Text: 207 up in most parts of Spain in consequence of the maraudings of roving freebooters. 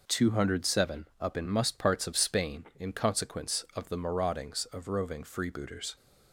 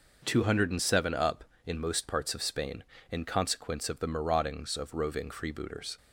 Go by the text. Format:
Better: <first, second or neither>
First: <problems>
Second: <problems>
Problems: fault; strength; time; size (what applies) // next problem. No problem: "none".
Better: second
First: says "must" for "most"; at 1.4 s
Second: none